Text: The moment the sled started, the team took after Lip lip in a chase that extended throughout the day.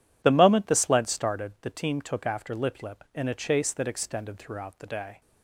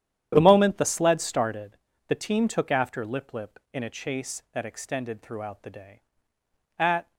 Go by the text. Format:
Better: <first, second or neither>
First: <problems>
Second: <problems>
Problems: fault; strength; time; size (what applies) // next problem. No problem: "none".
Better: first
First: none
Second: starts louder than the rest; strong; until 1.3 s; 10.5 dB // goes on to say "At"; slight; from 6.7 s on; 0.34 s long